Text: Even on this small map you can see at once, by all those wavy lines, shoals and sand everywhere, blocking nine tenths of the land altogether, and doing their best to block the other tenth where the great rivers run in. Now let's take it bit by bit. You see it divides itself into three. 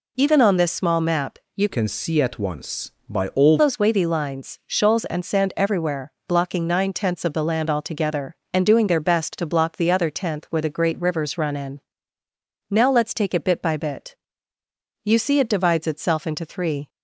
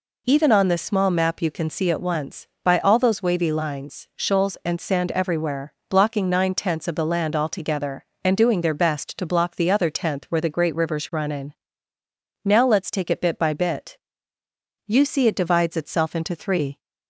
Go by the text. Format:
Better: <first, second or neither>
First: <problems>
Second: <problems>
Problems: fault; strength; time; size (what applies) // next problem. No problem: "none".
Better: second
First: pauses between "map" and "you"; slight; at 1.3 s; 0.18 s long // changes voice from "can" to "all"; from 1.6 to 3.5 s; 1.9 s long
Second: none